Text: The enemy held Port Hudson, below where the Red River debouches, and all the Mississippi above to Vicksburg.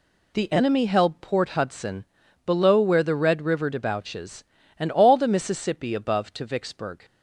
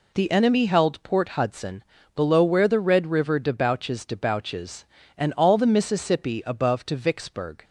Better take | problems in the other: first | says "debouches" twice; at 4.0 s

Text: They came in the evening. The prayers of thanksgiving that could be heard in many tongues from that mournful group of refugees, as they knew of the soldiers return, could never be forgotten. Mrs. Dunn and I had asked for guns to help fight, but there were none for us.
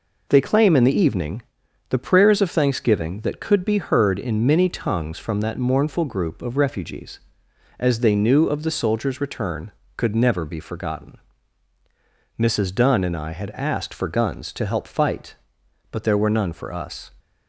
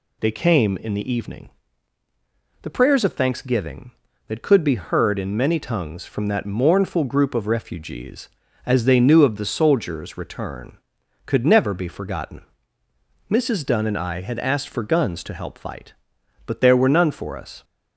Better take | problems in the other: second | says "claim" for "came"; at 0.4 s

